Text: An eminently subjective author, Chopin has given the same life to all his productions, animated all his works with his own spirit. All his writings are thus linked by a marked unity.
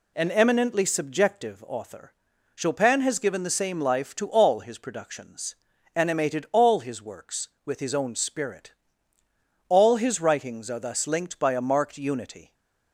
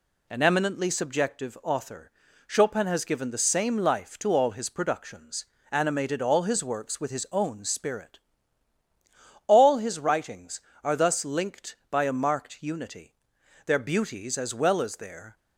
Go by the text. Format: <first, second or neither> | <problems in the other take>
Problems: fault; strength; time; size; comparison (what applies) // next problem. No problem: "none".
first | goes on to say "Their beauties as well as their"; strong; from 13.6 s on; 1.7 s long